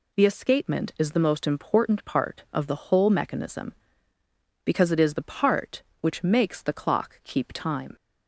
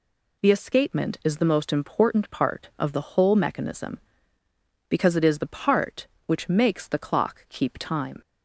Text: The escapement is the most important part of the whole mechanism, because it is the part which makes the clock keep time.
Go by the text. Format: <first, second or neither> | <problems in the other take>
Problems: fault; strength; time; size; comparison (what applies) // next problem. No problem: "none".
neither | none